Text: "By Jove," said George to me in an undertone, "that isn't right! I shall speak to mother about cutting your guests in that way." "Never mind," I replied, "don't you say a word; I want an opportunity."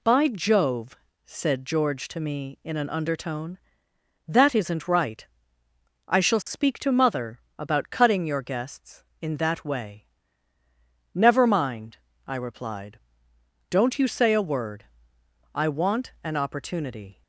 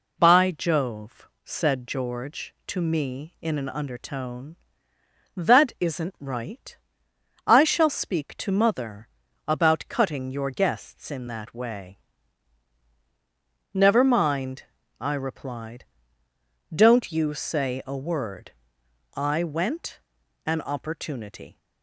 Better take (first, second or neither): first